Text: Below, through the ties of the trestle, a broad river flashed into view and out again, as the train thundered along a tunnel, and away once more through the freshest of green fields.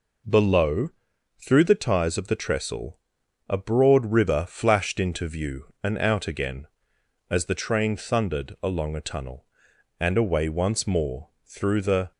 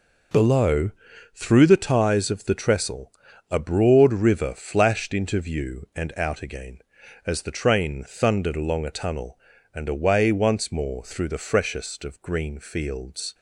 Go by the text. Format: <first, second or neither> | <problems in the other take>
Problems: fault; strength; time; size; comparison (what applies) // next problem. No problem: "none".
second | stops before "freshest of green fields"; at 12.1 s